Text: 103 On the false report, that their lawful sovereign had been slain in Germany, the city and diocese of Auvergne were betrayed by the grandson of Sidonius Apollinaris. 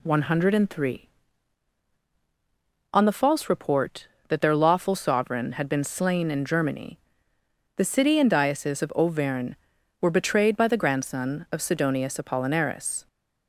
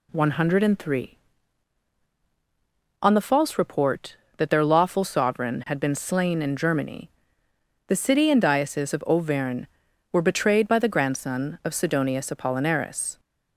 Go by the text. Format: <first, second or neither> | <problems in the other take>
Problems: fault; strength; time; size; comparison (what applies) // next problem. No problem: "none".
neither | none